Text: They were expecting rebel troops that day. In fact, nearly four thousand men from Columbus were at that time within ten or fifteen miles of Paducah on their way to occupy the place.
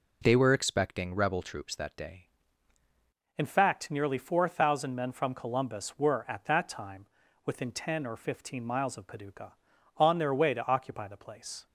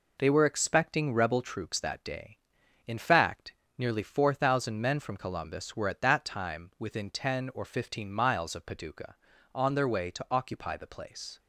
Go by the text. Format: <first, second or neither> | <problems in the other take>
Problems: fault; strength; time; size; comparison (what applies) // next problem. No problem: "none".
second | changes voice at "In"; from 3.3 s on; 8.3 s long // pauses between "time" and "within"; at 7.0 s; 0.38 s long